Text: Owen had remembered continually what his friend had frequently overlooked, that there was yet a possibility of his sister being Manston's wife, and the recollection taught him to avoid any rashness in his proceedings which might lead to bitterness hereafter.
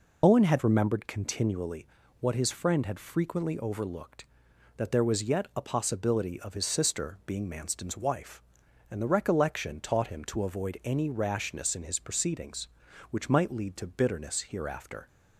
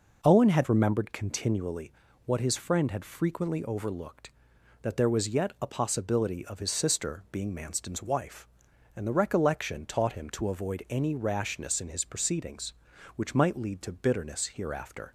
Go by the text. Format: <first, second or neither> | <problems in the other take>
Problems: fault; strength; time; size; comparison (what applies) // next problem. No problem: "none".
second | loses the start of "Owen"; at 0.2 s; 50 ms // pauses between "continually" and "what"; slight; at 1.8 s; 0.32 s long; slight in the second